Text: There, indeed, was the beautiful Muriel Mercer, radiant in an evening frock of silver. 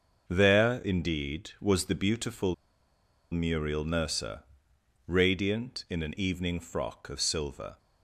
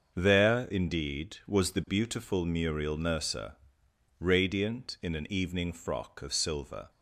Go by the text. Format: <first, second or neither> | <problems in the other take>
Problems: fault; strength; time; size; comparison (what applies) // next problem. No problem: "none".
second | starts louder than the rest; until 1.2 s; 6.5 dB; also in the second // pauses between "beautiful" and "Muriel"; noticeable; at 2.5 s; 0.78 s long